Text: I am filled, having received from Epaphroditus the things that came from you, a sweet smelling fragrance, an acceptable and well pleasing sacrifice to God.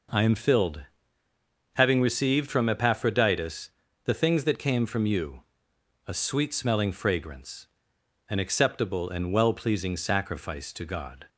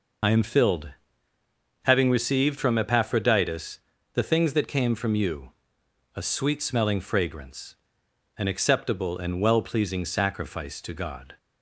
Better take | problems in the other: first | loses the start of "I"; at 0.2 s; 65 ms // pauses between "Epaphroditus" and "the"; slight; at 3.7 s; 0.36 s long; slight in the first

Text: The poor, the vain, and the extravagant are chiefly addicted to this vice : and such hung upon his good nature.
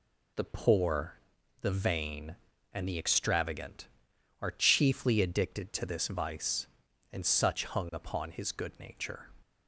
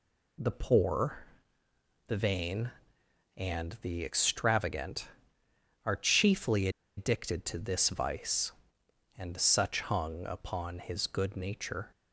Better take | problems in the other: first | pauses between "chiefly" and "addicted"; slight; at 6.6 s; 0.28 s long

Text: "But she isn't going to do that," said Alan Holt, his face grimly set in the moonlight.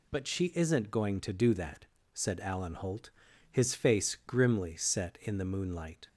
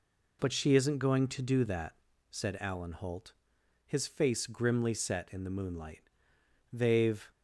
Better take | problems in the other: first | goes on to say "They've"; from 6.7 s on; 0.58 s long

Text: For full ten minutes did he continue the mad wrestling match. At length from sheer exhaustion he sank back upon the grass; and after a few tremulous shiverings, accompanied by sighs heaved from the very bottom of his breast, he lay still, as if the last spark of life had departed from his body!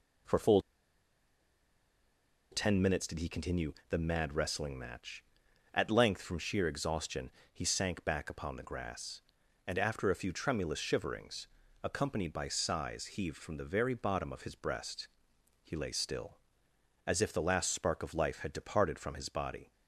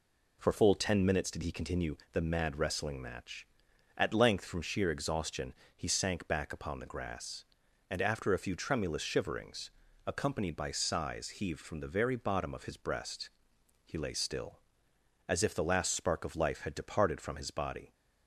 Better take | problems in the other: second | pauses between "full" and "ten"; strong; at 0.5 s; 1.9 s long // pauses between "continue" and "the"; slight; at 3.7 s; 0.16 s long; slight in the second // pauses between "exhaustion" and "he"; slight; at 7.2 s; 0.22 s long; slight in the second

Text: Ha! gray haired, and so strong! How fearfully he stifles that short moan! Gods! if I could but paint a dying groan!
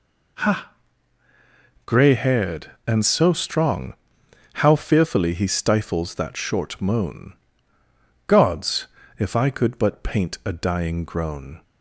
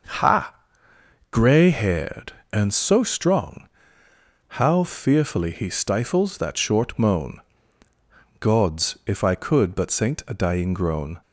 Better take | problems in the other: first | starts louder than the rest; until 1.9 s; 6 dB // says "saint" for "paint"; at 9.8 s

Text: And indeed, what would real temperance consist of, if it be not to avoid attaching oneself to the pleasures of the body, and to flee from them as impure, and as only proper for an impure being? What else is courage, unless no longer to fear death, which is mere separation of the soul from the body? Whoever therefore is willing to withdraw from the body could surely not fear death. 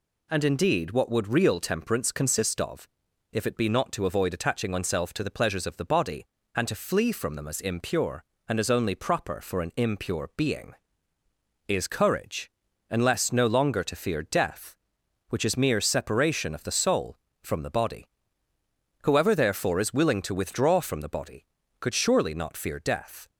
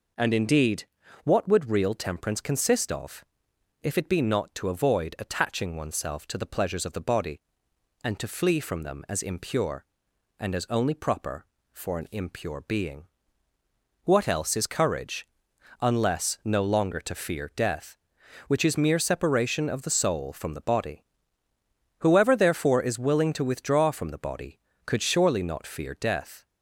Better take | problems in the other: second | skips "What else"; at 11.2 s

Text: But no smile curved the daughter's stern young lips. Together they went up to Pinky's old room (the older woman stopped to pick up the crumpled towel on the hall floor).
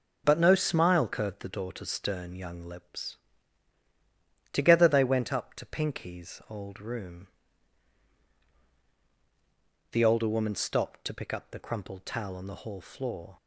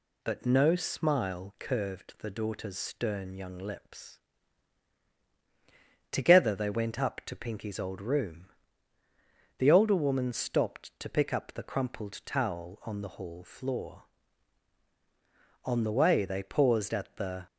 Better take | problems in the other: first | goes on to say "On the way they paused at the"; strong; from 15.6 s on; 1.8 s long

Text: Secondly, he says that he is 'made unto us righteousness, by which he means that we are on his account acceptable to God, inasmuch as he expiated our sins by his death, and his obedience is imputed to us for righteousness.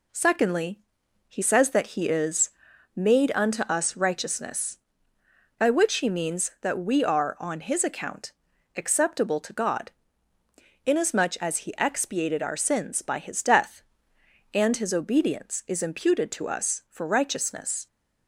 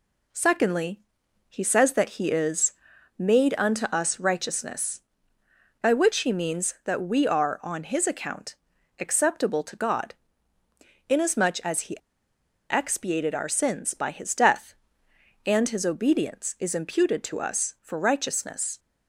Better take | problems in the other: first | pauses between "is" and "made"; at 2.7 s; 0.44 s long; also in the first // pauses between "account" and "acceptable"; at 8.5 s; 0.44 s long; also in the first // pauses between "he" and "expiated"; noticeable; at 11.9 s; 0.73 s long

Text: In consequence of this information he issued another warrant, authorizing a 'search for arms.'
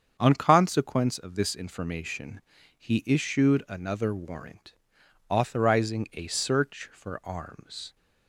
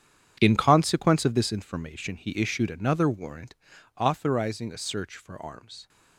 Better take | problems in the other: second | starts louder than the rest; strong; until 1.2 s; 7.5 dB; strong in the second // says "On" for "In"; at 0.1 s // pauses between "information" and "he"; at 2.3 s; 0.38 s long

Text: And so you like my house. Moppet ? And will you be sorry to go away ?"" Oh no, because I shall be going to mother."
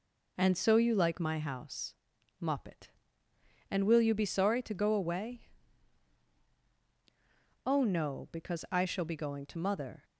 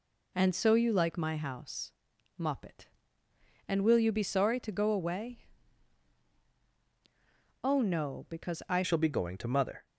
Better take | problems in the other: first | changes voice at "shall"; from 8.8 s on; 1.0 s long

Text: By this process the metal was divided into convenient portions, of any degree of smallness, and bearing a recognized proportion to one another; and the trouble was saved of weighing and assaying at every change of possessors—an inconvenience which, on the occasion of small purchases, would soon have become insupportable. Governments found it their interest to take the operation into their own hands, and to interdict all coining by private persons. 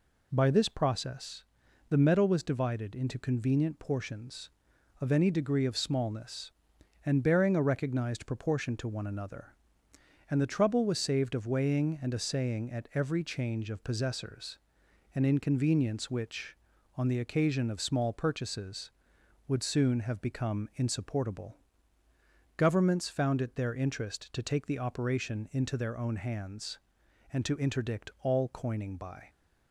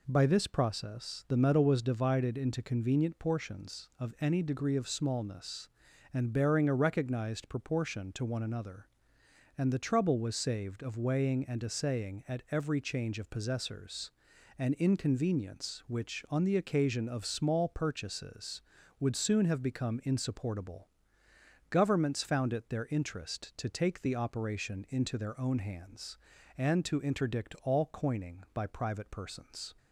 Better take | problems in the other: second | pauses between "process" and "the"; at 1.4 s; 0.44 s long // stops before "private persons"; at 29.2 s

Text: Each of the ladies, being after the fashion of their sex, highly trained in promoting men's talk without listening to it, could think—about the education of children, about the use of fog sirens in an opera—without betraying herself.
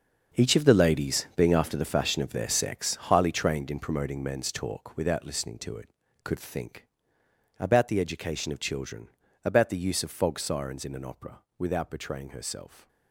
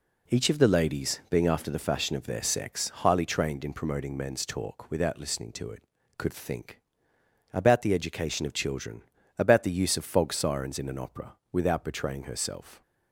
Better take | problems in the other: second | gets quieter; strong; throughout; 11.5 dB

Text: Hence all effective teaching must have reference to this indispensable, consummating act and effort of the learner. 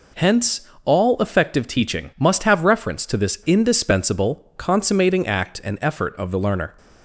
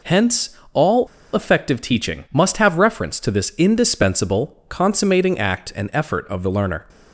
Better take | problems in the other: first | pauses between "Hence" and "all"; slight; at 0.5 s; 0.16 s long; slight in the first // pauses between "all" and "effective"; slight; at 1.0 s; 0.26 s long

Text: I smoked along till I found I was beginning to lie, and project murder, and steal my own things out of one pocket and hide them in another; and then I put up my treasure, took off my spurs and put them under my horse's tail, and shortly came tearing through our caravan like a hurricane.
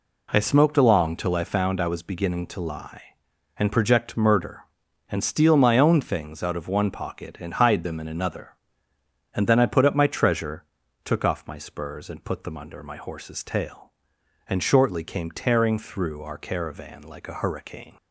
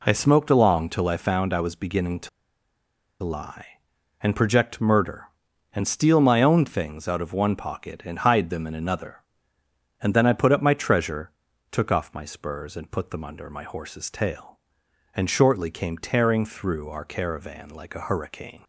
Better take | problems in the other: first | pauses between "to" and "lie"; noticeable; at 2.2 s; 0.94 s long

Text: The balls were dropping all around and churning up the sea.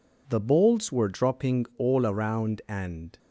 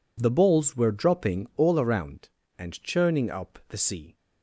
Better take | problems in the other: second | stops before "churning up the sea"; at 3.1 s

